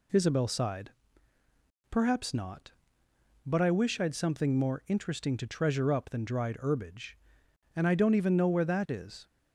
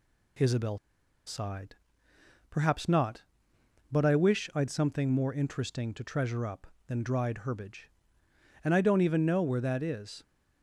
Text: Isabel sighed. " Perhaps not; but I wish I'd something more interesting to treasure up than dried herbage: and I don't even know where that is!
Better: first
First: none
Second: pauses between "Isabel" and "sighed"; noticeable; at 0.7 s; 0.49 s long

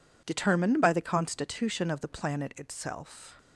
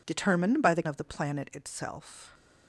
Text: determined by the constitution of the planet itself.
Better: first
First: none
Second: skips "constitution"; at 0.8 s

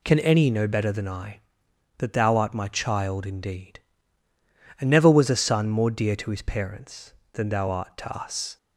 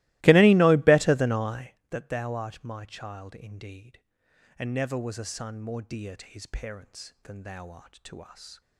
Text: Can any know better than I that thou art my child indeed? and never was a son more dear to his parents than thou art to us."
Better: first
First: none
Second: starts louder than the rest; strong; until 1.8 s; 20 dB

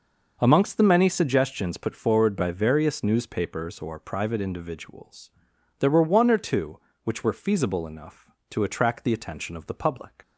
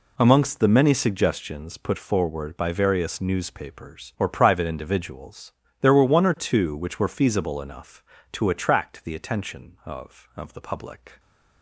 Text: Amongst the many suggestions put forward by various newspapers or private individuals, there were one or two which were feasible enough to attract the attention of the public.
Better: first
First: none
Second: says "of" twice; at 10.3 s

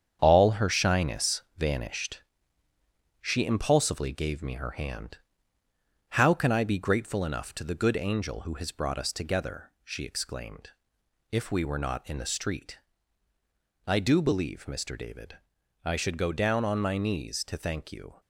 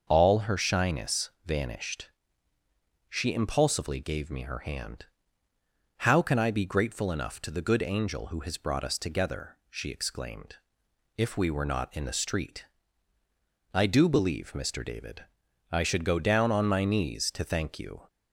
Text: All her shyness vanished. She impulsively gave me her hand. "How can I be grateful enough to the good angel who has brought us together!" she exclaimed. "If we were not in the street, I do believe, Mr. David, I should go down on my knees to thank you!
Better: second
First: gets quieter; throughout; 7 dB // starts louder than the rest; strong; until 1.2 s; 8 dB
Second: starts louder than the rest; until 1.1 s; 6.5 dB

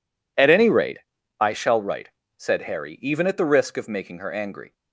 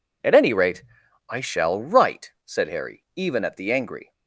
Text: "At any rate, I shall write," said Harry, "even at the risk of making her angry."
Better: first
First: none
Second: skips "risk of making her"; at 3.7 s

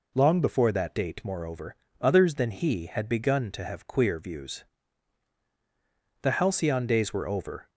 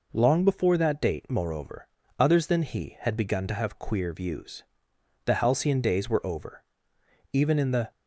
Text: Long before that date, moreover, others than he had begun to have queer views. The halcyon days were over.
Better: first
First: none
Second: goes on to say "Even in the"; from 7.3 s on; 0.58 s long

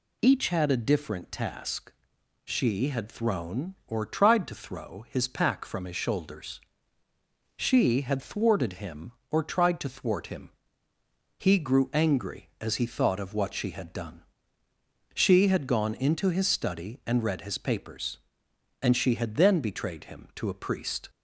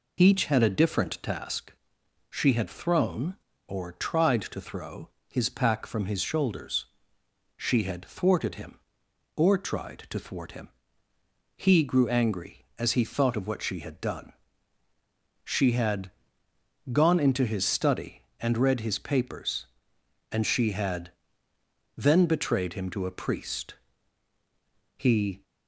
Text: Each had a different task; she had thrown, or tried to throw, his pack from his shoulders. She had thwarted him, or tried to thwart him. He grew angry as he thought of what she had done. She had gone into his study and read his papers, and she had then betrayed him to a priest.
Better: first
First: none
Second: pauses between "had" and "gone"; noticeable; at 16.1 s; 0.80 s long // pauses between "had" and "then"; noticeable; at 21.1 s; 0.84 s long // goes on to say "He"; slight; from 24.9 s on; 0.46 s long

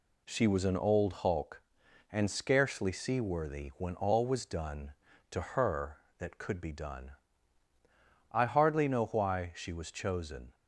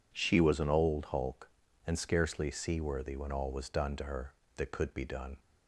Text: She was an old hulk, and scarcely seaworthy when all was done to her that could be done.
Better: second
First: goes on to say "I hardly know why she was chosen"; strong; from 8.3 s on; 2.2 s long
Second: none

